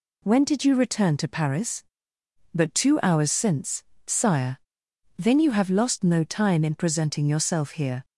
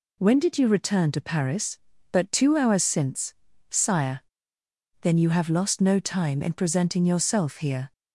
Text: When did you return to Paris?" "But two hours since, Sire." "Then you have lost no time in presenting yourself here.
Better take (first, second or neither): neither